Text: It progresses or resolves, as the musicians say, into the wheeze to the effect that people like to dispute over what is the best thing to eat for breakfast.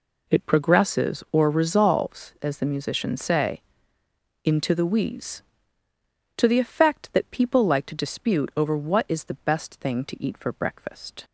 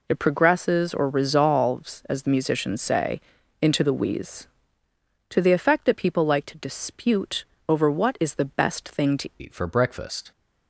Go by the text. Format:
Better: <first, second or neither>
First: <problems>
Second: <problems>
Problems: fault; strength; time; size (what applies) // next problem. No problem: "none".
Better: first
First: none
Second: pauses between "dispute" and "over"; slight; at 7.4 s; 0.22 s long // changes voice at "eat"; from 9.3 s on; 1.0 s long